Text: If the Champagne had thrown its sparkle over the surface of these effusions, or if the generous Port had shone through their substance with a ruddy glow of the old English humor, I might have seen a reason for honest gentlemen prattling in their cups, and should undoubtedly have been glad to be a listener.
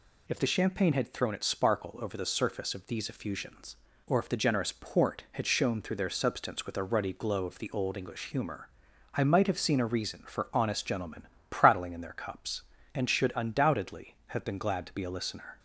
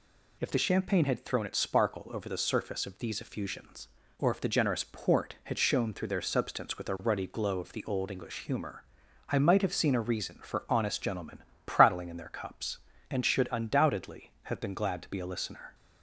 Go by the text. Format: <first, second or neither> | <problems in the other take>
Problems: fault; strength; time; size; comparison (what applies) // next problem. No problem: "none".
neither | pauses between "gentlemen" and "prattling"; slight; the same in both